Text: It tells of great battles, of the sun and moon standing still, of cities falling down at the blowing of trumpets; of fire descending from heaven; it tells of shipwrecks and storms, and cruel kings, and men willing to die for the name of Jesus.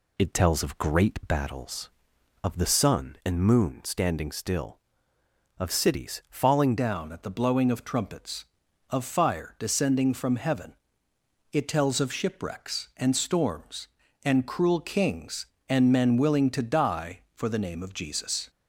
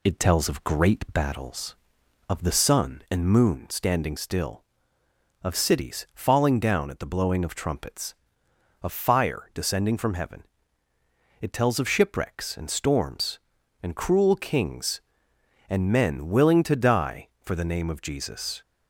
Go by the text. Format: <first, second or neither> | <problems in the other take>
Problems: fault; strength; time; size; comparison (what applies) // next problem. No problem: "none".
second | changes voice at "down"; from 6.7 s on; 11.7 s long